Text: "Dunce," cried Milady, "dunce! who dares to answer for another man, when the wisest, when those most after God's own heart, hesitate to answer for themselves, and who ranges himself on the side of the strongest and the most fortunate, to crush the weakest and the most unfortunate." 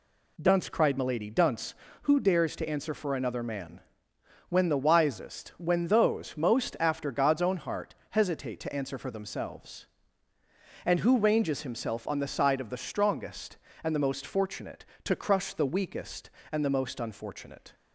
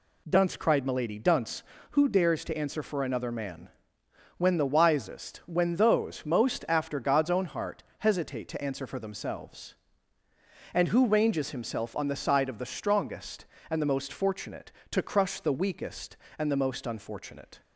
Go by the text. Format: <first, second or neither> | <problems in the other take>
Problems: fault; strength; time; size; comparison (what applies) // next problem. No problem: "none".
neither | none